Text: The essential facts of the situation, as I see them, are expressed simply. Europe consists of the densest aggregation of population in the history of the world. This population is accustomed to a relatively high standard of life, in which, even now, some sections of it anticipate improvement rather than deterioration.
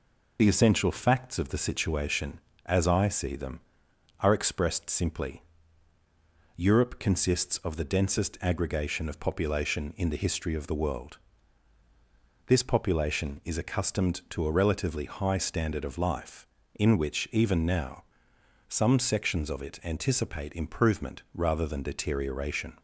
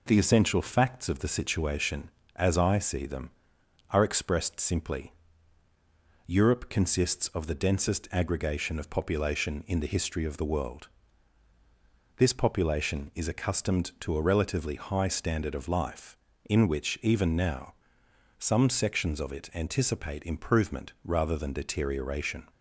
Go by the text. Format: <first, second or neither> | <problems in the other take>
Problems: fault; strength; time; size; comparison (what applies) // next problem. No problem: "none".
second | loses the start of "The"; at 0.3 s; 40 ms